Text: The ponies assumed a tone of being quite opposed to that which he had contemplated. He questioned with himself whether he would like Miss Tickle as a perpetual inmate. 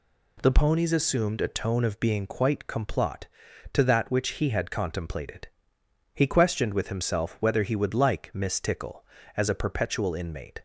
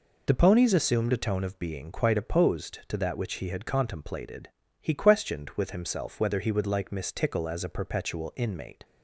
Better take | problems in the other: second | says "complot" for "opposed"; at 2.6 s

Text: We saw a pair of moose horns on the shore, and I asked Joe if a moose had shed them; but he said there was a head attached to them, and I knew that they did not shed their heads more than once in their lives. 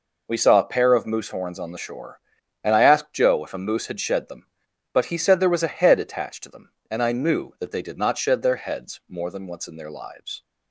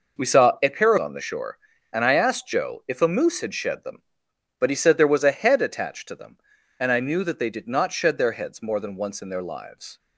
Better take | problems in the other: first | skips "of moose horns"; at 0.9 s

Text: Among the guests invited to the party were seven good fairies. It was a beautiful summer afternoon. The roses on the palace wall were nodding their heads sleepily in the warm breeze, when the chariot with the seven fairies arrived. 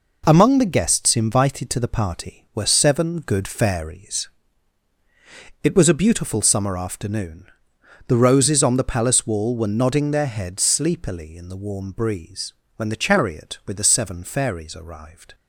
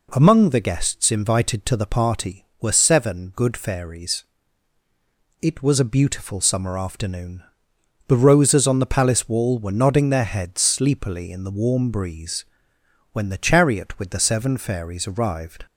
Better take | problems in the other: neither | none

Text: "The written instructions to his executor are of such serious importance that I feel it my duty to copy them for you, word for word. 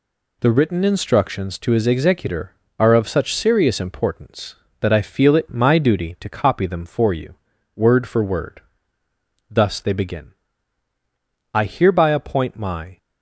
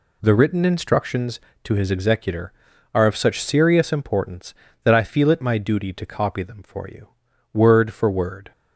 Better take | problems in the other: second | goes on to say "Thus they begin I hereby appoint my"; strong; from 9.4 s on; 3.4 s long

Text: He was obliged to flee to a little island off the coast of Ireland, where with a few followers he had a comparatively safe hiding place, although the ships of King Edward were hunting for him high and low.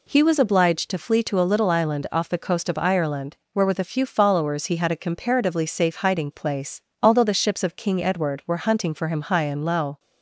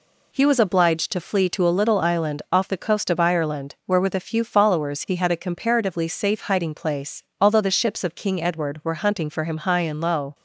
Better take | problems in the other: neither | none

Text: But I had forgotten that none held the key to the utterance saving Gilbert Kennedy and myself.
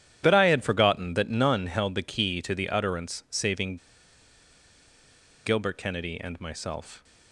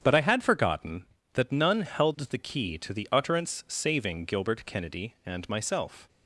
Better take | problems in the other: second | starts louder than the rest; strong; until 1.2 s; 10 dB; strong in the second // pauses between "saving" and "Gilbert"; strong; at 3.7 s; 1.6 s long

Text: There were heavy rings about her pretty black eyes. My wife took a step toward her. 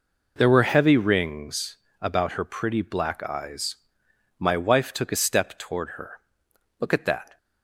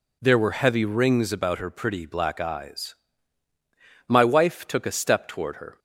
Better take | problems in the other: second | pauses between "rings" and "about"; slight; at 1.7 s; 0.22 s long // goes on to say "Look at that"; from 6.7 s on; 0.58 s long

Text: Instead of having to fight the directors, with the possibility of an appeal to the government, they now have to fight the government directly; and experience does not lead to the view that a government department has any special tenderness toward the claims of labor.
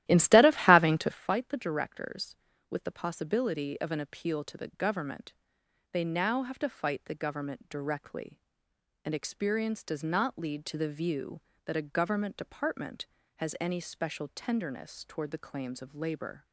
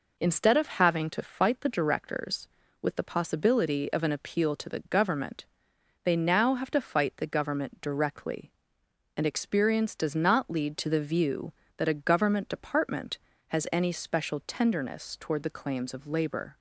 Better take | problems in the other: second | starts louder than the rest; strong; until 1.3 s; 14 dB

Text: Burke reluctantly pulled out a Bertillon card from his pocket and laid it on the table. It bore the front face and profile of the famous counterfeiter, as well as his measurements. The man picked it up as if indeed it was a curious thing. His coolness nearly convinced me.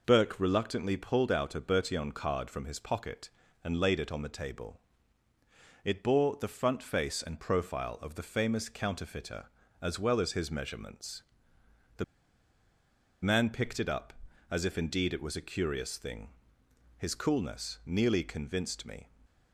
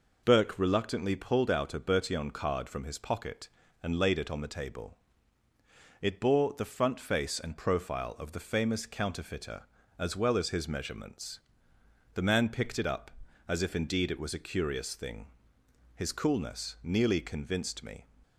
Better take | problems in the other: second | pauses between "The" and "man"; at 12.0 s; 1.1 s long

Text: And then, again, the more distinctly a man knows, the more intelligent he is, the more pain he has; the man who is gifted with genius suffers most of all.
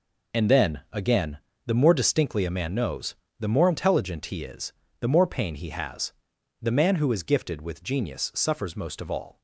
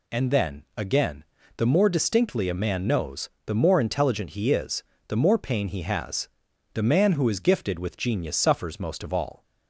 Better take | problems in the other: second | gets quieter; strong; throughout; 10.5 dB

